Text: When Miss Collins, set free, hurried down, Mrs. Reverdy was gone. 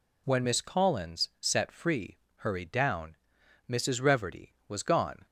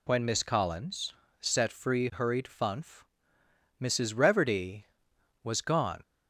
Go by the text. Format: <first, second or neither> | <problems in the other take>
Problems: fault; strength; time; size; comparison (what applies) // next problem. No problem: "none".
first | says "funf" for "down"; at 2.4 s